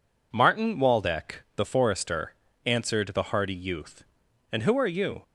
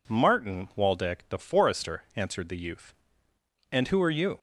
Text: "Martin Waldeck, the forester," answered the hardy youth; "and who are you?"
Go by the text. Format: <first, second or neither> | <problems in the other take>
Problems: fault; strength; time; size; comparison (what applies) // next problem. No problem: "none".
first | skips "hardy"; at 2.5 s